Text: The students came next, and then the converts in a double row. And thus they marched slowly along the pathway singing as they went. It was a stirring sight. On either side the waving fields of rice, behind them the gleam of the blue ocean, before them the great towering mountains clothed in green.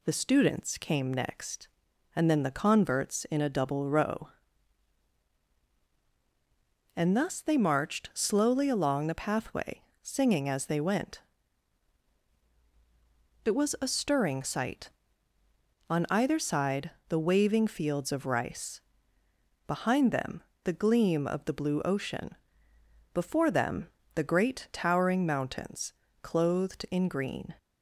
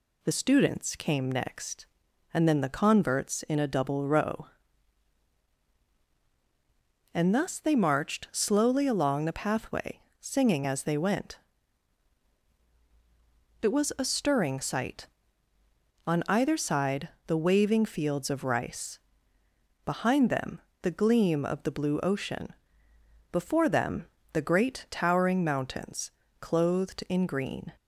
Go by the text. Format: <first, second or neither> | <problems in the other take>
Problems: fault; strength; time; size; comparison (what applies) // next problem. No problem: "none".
neither | pauses between "pathway" and "singing"; slight; the same in both // pauses between "side" and "the"; slight; the same in both // pauses between "them" and "the"; slight; the same in both // pauses between "them" and "the"; slight; the same in both // pauses between "mountains" and "clothed"; slight; the same in both